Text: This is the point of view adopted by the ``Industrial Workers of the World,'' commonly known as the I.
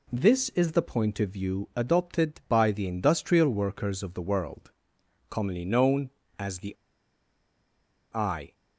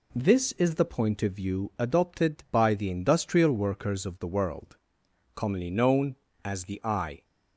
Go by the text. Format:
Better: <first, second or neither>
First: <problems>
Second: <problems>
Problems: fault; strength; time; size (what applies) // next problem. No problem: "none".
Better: second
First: pauses between "the" and "I"; strong; at 6.7 s; 1.3 s long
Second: none